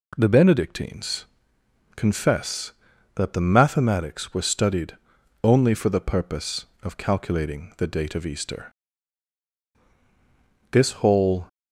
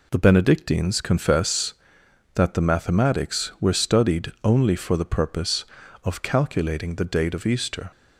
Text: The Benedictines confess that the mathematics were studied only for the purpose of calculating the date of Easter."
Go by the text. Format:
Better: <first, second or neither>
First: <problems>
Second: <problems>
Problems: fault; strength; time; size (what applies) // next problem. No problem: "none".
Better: second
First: pauses between "Benedictines" and "confess"; noticeable; at 1.2 s; 0.70 s long // pauses between "studied" and "only"; noticeable; at 4.9 s; 0.46 s long // goes on to say "This whole"; noticeable; from 10.6 s on; 0.78 s long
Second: none